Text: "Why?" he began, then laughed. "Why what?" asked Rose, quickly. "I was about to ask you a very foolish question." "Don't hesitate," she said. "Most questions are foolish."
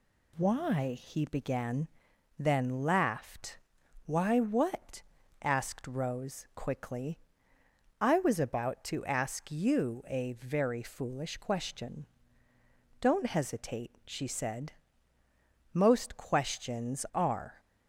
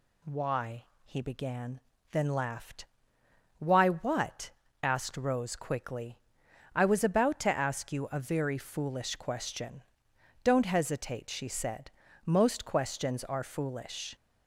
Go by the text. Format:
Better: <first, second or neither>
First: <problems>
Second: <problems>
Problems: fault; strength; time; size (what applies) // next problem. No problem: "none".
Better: second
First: stops before "foolish"; at 17.5 s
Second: none